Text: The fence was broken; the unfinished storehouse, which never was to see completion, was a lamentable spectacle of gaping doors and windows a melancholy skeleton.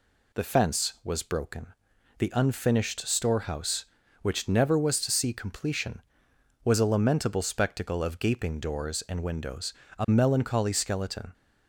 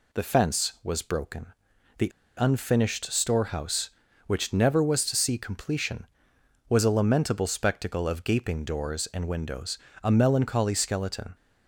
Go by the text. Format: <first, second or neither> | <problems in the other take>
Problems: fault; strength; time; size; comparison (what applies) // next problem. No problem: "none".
first | pauses between "the" and "unfinished"; slight; at 2.1 s; 0.29 s long // pauses between "windows" and "a"; slight; at 9.7 s; 0.24 s long; slight in the first